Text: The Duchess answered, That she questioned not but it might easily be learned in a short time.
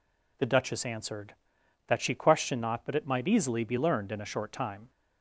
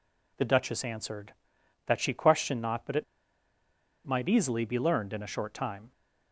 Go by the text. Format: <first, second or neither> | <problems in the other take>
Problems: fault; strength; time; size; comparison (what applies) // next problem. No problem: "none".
first | pauses between "it" and "might"; at 3.0 s; 1.0 s long